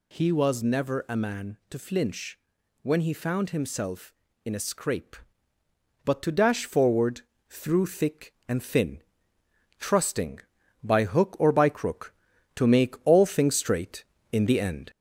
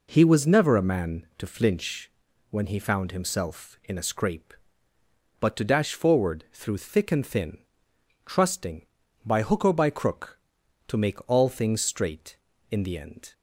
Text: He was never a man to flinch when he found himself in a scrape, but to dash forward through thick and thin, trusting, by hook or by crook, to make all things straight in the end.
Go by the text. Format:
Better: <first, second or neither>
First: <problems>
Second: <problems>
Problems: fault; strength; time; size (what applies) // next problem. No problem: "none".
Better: second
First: gets louder; slight; throughout; 2 dB // pauses between "flinch" and "when"; noticeable; at 2.3 s; 0.46 s long // pauses between "forward" and "through"; slight; at 7.1 s; 0.28 s long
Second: pauses between "flinch" and "when"; at 2.0 s; 0.40 s long